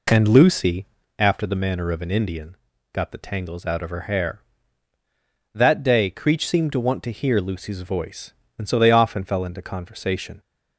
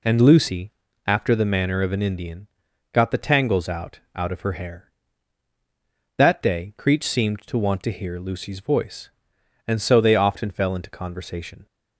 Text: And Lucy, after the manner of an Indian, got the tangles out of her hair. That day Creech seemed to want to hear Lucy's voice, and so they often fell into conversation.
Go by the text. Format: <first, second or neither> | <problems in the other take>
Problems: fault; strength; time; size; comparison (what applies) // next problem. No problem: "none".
first | says "out" twice; at 4.1 s